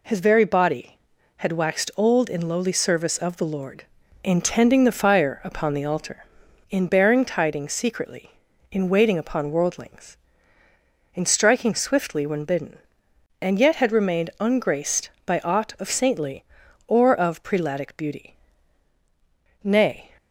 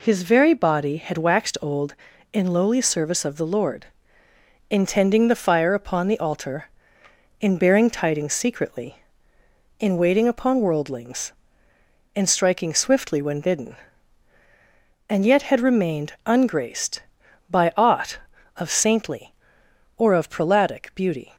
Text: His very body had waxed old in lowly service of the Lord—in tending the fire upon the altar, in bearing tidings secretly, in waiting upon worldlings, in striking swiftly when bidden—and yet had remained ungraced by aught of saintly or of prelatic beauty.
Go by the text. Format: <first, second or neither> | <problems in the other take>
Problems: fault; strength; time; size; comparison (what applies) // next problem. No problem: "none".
second | goes on to say "Nay"; slight; from 19.6 s on; 0.48 s long